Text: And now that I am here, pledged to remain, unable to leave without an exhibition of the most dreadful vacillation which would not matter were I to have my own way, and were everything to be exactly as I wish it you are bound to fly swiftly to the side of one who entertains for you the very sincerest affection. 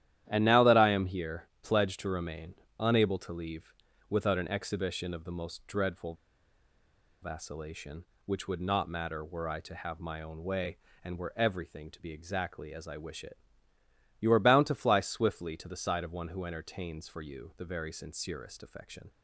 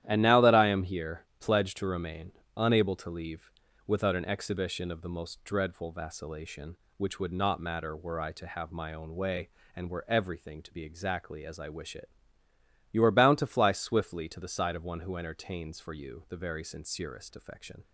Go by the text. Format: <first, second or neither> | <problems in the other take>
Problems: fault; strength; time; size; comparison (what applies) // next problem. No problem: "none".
second | starts louder than the rest; strong; until 1.3 s; 11.5 dB; strong in the second // pauses between "leave" and "without"; slight; at 3.7 s; 0.36 s long; slight in the second // pauses between "dreadful" and "vacillation"; at 6.1 s; 1.0 s long // pauses between "it" and "you"; noticeable; at 13.3 s; 0.84 s long; noticeable in the second